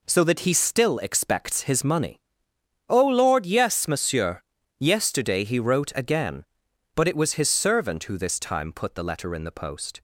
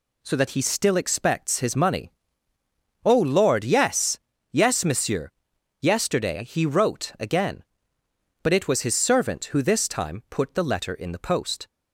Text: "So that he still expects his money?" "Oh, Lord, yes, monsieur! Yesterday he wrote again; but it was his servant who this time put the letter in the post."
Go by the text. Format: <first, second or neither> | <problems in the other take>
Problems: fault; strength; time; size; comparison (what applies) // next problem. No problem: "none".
first | says "yes" twice; at 4.5 s